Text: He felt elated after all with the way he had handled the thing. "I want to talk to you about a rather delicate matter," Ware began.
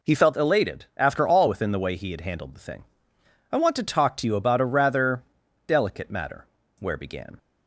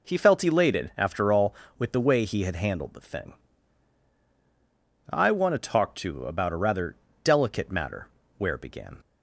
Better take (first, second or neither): second